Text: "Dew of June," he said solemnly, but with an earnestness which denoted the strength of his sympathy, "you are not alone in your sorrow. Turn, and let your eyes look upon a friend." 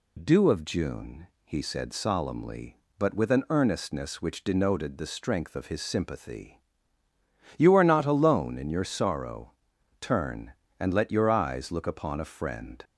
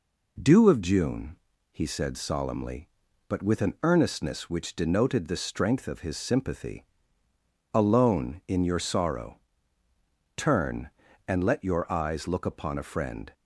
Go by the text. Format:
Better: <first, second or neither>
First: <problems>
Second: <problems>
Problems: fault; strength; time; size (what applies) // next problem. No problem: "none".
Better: first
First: none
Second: skips "you are not"; at 7.2 s